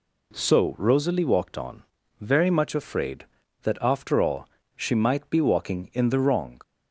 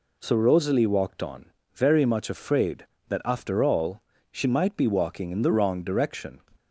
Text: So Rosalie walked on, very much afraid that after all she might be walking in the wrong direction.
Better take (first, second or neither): second